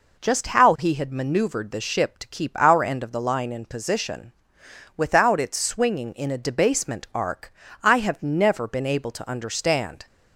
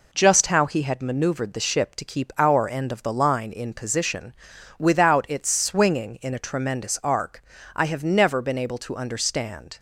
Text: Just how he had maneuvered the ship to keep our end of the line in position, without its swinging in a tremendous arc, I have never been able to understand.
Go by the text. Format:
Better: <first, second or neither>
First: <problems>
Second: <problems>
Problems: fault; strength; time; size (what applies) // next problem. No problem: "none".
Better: second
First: says "debasement" for "tremendous"; at 6.3 s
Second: none